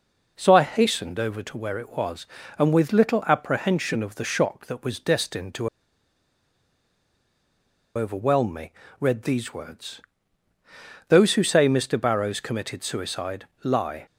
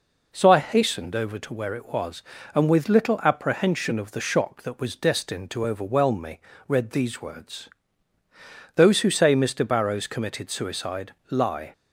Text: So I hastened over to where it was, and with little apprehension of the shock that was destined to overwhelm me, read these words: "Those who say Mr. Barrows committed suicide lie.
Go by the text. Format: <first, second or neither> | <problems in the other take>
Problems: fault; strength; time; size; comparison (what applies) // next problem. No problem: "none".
second | pauses between "to" and "overwhelm"; strong; at 5.6 s; 2.2 s long // pauses between "suicide" and "lie"; slight; at 13.4 s; 0.16 s long; slight in the second